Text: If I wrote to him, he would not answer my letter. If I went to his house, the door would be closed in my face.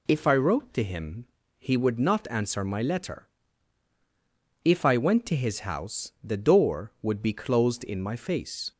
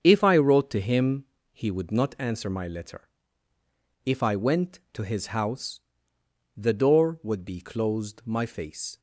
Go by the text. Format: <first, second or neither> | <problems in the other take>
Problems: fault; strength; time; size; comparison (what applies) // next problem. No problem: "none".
first | starts louder than the rest; strong; until 1.0 s; 7 dB // skips "in"; at 8.2 s